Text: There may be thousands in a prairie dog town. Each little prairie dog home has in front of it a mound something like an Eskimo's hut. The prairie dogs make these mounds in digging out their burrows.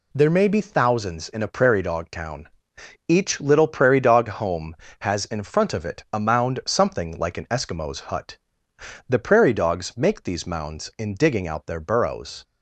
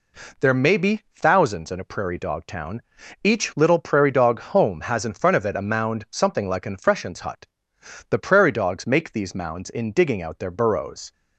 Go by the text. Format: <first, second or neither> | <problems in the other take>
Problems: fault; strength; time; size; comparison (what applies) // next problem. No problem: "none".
first | says "Freshens" for "Eskimo's"; at 6.7 s